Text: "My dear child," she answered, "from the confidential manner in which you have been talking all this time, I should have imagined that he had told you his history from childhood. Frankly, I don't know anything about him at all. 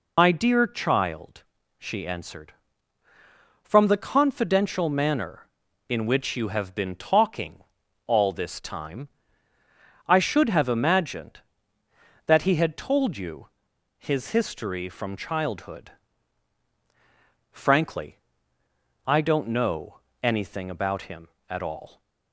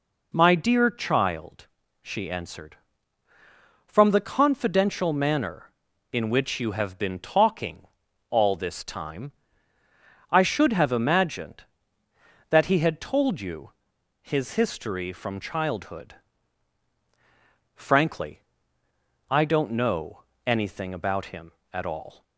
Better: second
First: loses the start of "My"; at 0.1 s; 75 ms // pauses between "talking" and "all"; at 7.6 s; 0.44 s long // pauses between "you" and "his"; noticeable; at 13.4 s; 0.50 s long // pauses between "know" and "anything"; slight; at 20.0 s; 0.22 s long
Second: pauses between "talking" and "all"; at 7.8 s; 0.44 s long // pauses between "you" and "his"; noticeable; at 13.7 s; 0.50 s long // pauses between "know" and "anything"; slight; at 20.2 s; 0.22 s long

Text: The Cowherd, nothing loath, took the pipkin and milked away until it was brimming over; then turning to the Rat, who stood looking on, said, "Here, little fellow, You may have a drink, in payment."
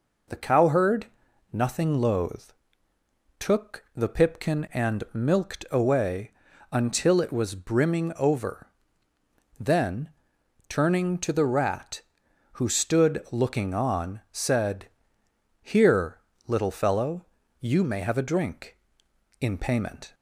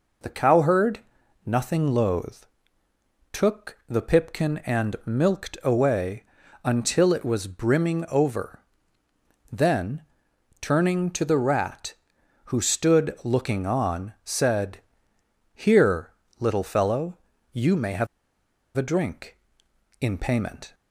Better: first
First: pauses between "away" and "until"; at 6.2 s; 0.42 s long // pauses between "then" and "turning"; noticeable; at 10.0 s; 0.58 s long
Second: pauses between "away" and "until"; at 6.2 s; 0.42 s long // pauses between "then" and "turning"; noticeable; at 10.0 s; 0.58 s long // pauses between "have" and "a"; noticeable; at 18.0 s; 0.70 s long

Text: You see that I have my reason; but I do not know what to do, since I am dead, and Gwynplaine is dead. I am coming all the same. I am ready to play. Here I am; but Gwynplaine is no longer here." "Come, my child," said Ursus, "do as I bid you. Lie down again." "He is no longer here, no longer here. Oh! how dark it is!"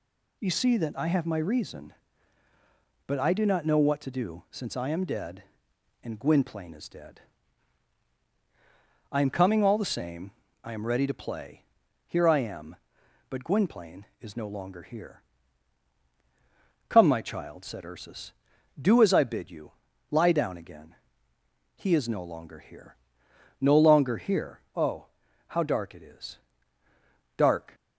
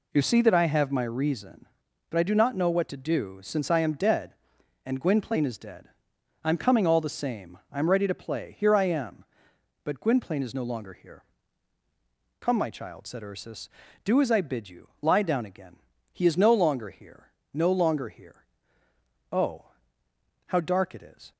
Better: second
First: goes on to say "Dark"; slight; from 27.3 s on; 0.38 s long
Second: none

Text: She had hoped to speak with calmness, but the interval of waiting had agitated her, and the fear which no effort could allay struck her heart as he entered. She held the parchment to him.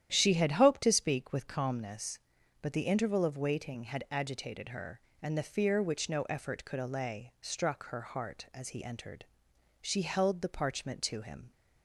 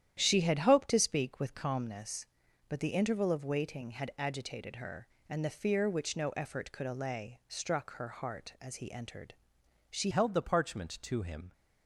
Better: first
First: starts louder than the rest; strong; until 1.1 s; 10.5 dB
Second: starts louder than the rest; strong; until 1.2 s; 10.5 dB // changes voice at "held"; from 10.1 s on; 1.4 s long

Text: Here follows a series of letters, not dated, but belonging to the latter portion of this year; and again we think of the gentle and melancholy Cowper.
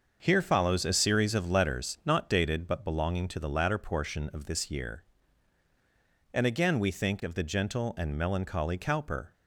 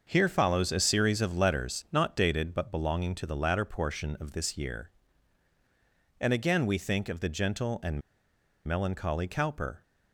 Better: first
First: starts louder than the rest; until 1.2 s; 6.5 dB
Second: starts louder than the rest; until 1.1 s; 6.5 dB // pauses between "and" and "melancholy"; noticeable; at 8.0 s; 0.65 s long

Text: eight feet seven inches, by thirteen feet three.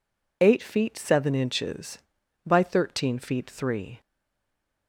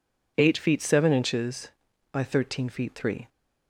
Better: second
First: stays silent after the last word; slight; from 4.0 s on; 0.8 s long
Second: none

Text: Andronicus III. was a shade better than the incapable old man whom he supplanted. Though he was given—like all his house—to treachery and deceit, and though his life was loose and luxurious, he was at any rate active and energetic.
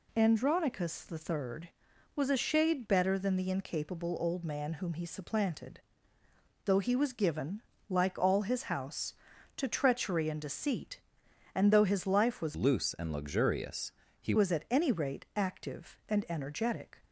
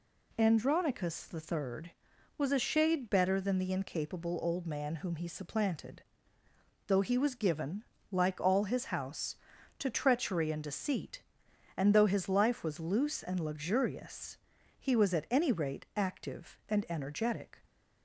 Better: second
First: changes voice from "loose" to "he"; from 12.5 to 14.3 s; 1.8 s long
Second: none

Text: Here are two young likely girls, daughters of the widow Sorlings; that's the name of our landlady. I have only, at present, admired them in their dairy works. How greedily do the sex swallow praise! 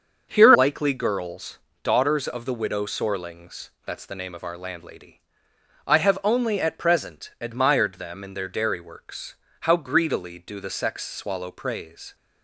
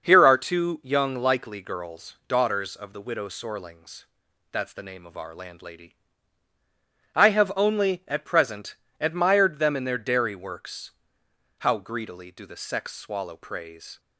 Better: second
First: starts louder than the rest; until 1.3 s; 6.5 dB // skips "are two young"; at 0.5 s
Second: starts louder than the rest; noticeable; until 1.0 s; 6 dB

